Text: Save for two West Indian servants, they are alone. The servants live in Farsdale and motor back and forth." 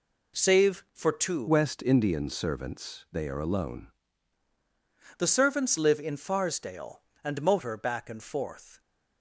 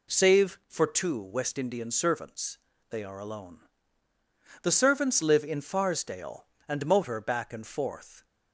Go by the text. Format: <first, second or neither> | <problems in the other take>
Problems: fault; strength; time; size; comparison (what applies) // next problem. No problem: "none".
second | changes voice from "West" to "alone"; from 1.4 to 3.8 s; 2.4 s long